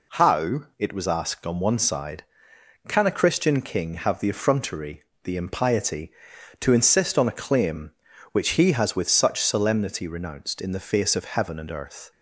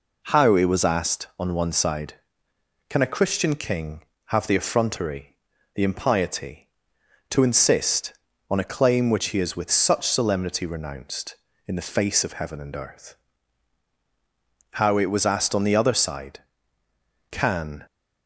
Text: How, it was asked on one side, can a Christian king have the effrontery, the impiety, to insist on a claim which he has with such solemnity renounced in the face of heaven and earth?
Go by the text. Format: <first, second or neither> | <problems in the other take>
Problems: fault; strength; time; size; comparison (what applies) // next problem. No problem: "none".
first | goes on to say "How it was asked on the other side can"; strong; from 14.7 s on; 3.1 s long